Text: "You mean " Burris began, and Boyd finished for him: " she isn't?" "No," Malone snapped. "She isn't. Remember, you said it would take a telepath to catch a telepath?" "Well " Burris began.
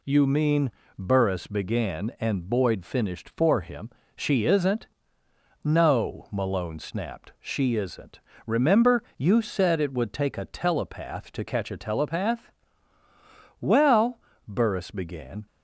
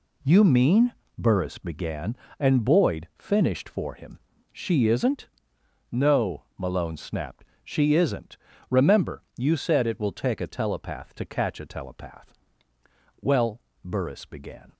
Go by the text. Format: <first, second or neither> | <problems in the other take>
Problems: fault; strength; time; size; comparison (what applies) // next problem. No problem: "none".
first | says "will" for "would"; at 9.9 s